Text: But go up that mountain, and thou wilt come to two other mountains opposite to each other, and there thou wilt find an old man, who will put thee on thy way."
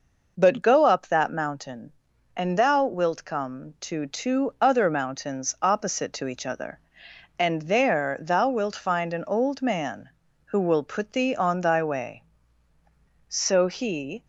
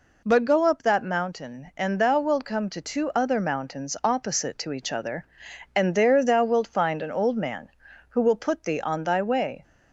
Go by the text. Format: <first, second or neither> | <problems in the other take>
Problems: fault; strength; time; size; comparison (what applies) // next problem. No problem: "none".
second | goes on to say "So he"; noticeable; from 13.2 s on; 0.96 s long